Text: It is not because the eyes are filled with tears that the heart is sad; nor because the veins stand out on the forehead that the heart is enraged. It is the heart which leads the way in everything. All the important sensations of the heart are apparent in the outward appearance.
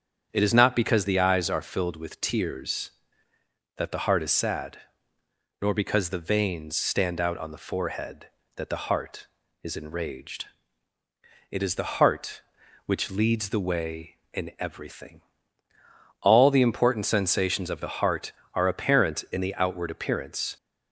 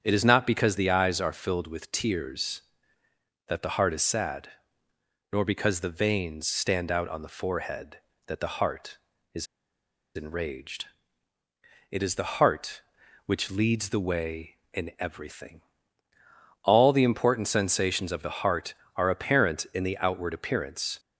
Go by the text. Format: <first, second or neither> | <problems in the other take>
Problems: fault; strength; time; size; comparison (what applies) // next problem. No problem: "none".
first | starts louder than the rest; strong; until 1.0 s; 8 dB; strong in the first // pauses between "is" and "enraged"; noticeable; at 9.4 s; 0.69 s long